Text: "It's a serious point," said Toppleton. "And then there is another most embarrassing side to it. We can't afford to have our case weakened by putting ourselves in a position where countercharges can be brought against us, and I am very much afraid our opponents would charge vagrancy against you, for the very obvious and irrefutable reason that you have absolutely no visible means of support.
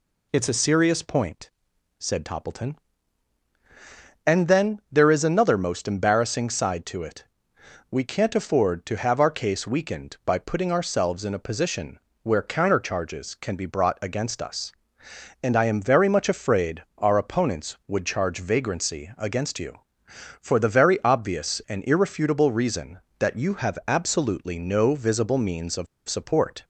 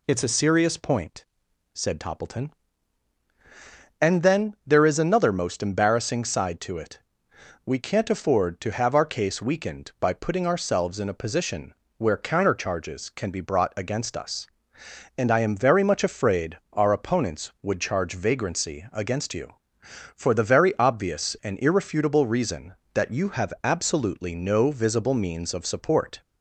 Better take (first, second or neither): second